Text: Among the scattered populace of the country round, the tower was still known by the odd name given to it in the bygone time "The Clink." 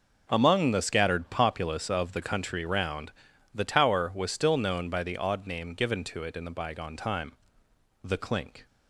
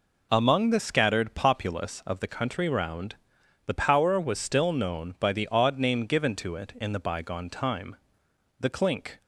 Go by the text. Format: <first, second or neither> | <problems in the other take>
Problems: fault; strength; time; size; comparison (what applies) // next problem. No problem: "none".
first | says "power" for "tower"; at 3.7 s // pauses between "time" and "The"; noticeable; at 7.9 s; 0.64 s long; noticeable in the first